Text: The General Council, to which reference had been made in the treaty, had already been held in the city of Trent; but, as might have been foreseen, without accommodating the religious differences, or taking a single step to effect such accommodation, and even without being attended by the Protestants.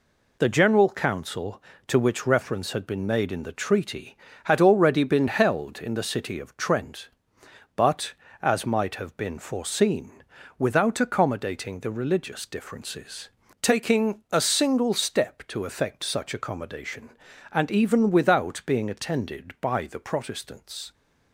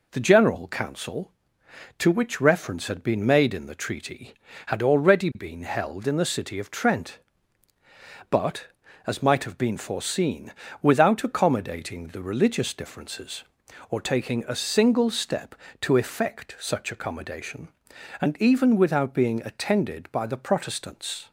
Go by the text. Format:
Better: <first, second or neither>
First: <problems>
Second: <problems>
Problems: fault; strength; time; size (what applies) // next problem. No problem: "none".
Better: second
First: skips "or"; at 13.4 s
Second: none